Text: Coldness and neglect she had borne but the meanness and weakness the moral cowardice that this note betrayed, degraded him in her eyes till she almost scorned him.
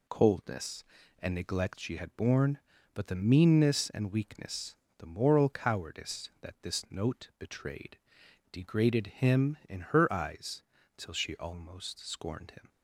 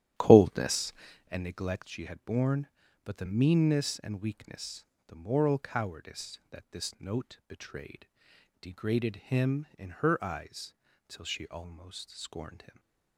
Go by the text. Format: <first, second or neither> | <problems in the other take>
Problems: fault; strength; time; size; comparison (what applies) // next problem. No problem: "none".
first | starts louder than the rest; strong; until 1.3 s; 12.5 dB // pauses between "weakness" and "the"; slight; at 4.8 s; 0.22 s long; slight in the first // pauses between "eyes" and "till"; slight; at 10.7 s; 0.34 s long; slight in the first